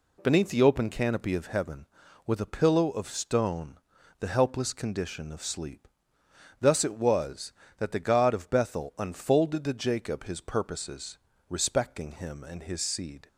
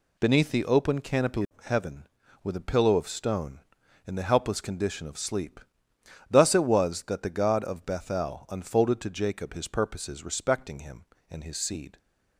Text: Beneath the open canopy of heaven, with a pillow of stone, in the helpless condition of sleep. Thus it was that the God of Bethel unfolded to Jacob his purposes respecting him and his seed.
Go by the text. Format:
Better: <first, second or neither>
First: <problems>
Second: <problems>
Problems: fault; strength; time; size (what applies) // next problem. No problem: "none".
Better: second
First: skips "in"; at 3.9 s // pauses between "purposes" and "respecting"; slight; at 11.1 s; 0.30 s long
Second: none